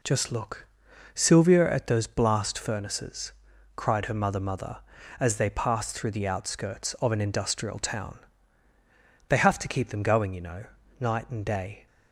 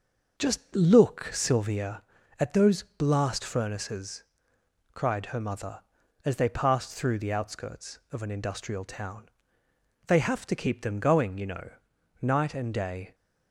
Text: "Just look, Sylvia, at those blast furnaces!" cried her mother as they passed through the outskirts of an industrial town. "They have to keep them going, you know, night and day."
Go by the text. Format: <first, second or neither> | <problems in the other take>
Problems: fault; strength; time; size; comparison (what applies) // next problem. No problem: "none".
second | says "mother" twice; at 4.3 s